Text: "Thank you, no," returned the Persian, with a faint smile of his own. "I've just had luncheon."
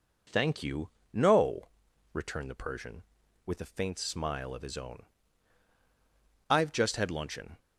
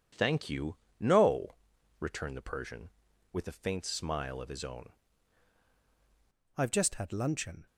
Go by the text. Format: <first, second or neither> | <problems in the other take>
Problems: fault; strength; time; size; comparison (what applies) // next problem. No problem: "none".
first | changes voice at "I've"; from 6.5 s on; 1.1 s long